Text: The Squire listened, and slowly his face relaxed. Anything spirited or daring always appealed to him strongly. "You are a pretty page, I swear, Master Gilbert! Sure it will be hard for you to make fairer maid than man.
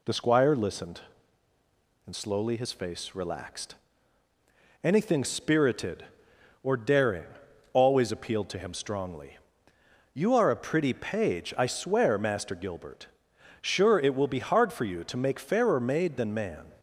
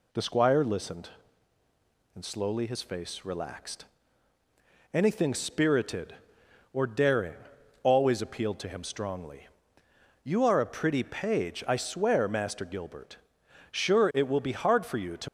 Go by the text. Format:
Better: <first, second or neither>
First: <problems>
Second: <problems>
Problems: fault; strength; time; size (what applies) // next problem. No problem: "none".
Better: first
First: pauses between "daring" and "always"; noticeable; at 7.2 s; 0.46 s long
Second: pauses between "daring" and "always"; noticeable; at 7.3 s; 0.46 s long // stops before "make fairer maid than man"; at 15.2 s